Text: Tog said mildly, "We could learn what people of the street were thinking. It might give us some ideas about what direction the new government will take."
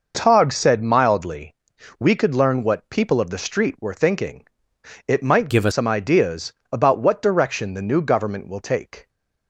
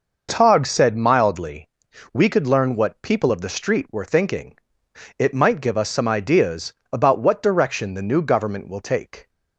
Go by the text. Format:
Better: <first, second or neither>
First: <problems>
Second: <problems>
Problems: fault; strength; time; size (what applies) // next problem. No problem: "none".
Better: second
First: changes voice from "give" to "us"; from 5.4 to 5.7 s; 0.3 s long // pauses between "ideas" and "about"; slight; at 6.5 s; 0.18 s long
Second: pauses between "ideas" and "about"; slight; at 6.7 s; 0.18 s long